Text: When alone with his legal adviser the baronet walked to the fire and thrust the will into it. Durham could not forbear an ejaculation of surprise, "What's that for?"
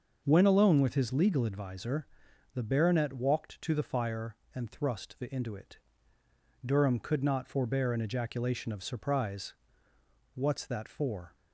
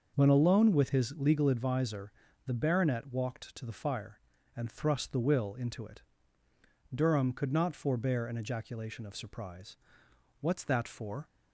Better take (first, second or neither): second